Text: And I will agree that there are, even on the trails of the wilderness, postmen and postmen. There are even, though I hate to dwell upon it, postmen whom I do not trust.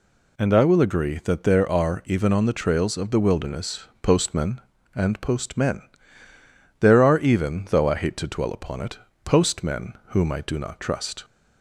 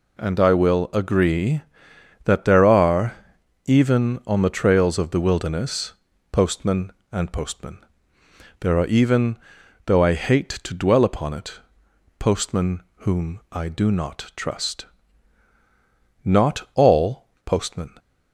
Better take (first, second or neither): first